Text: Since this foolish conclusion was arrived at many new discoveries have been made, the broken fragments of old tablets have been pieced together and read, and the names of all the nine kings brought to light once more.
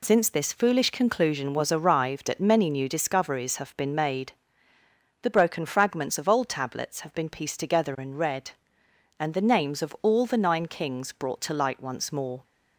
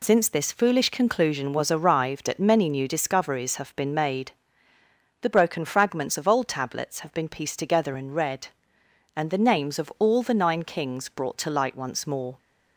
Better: neither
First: none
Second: none

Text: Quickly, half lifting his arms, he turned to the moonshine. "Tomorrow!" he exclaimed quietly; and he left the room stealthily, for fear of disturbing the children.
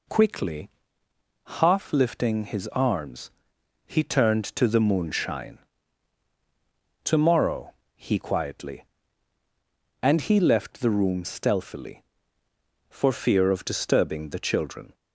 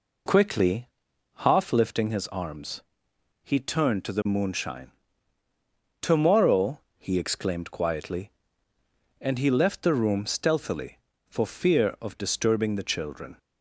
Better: second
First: skips "exclaimed"; at 8.1 s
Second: none

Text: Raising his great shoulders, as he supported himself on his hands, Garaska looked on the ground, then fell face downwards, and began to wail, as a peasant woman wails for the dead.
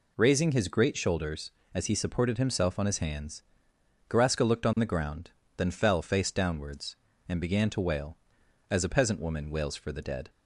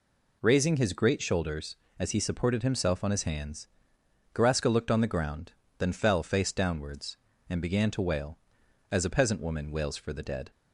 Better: neither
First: none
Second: none

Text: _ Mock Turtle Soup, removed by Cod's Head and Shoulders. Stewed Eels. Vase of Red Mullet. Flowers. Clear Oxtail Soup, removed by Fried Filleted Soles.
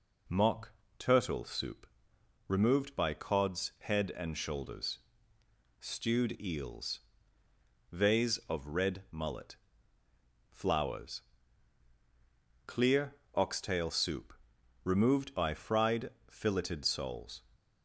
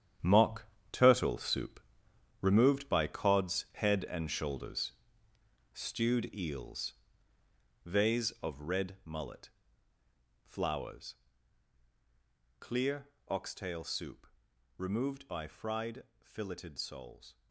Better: first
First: pauses between "Mock" and "Turtle"; slight; at 0.7 s; 0.24 s long // pauses between "Clear" and "Oxtail"; slight; at 13.1 s; 0.22 s long // pauses between "Fried" and "Filleted"; slight; at 16.0 s; 0.20 s long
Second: gets quieter; strong; throughout; 11 dB // pauses between "Mock" and "Turtle"; slight; at 0.6 s; 0.24 s long // pauses between "Clear" and "Oxtail"; slight; at 13.0 s; 0.22 s long // pauses between "Fried" and "Filleted"; slight; at 16.0 s; 0.20 s long

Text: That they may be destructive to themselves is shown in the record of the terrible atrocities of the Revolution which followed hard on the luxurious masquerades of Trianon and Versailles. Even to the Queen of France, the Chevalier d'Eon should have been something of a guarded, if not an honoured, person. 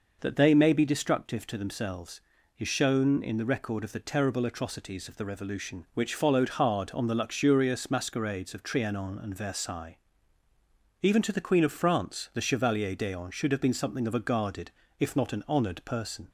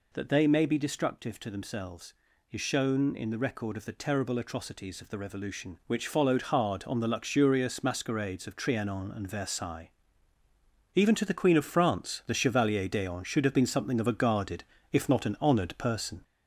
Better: first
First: none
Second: gets louder; noticeable; throughout; 4.5 dB

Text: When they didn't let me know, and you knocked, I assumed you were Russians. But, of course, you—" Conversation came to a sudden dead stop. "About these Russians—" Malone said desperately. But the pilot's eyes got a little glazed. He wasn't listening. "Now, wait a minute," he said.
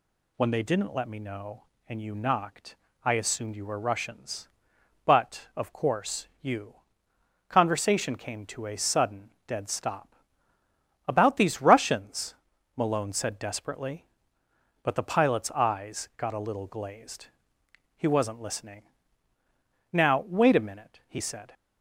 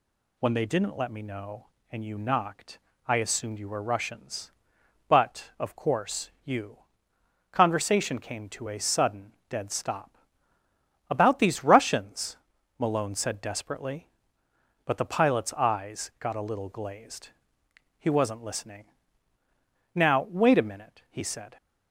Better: neither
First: pauses between "sudden" and "dead"; slight; at 9.3 s; 0.16 s long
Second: pauses between "sudden" and "dead"; slight; at 9.3 s; 0.16 s long

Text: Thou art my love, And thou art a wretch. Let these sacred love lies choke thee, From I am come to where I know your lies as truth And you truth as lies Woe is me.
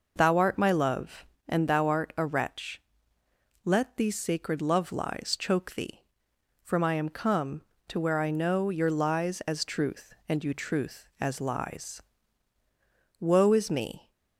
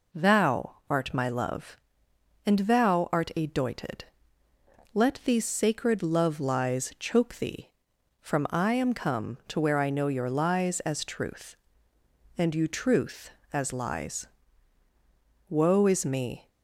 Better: first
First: pauses between "lies" and "Woe"; at 12.0 s; 1.1 s long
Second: says "doited" for "wretch"; at 3.4 s // pauses between "lies" and "Woe"; at 14.2 s; 1.2 s long

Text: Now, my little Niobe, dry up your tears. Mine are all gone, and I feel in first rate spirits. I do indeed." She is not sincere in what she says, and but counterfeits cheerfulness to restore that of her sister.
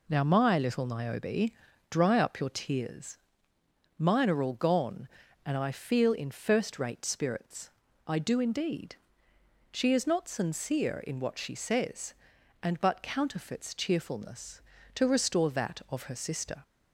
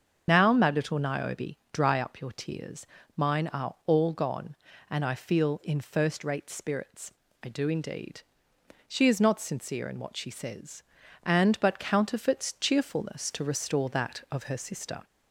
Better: first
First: none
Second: loses the start of "Now"; at 0.2 s; 25 ms // starts louder than the rest; until 1.2 s; 7 dB

